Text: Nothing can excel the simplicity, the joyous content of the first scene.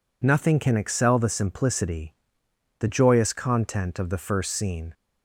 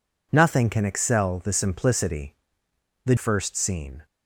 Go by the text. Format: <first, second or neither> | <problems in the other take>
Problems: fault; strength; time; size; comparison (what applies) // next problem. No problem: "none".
first | skips "joyous content of the"; at 3.1 s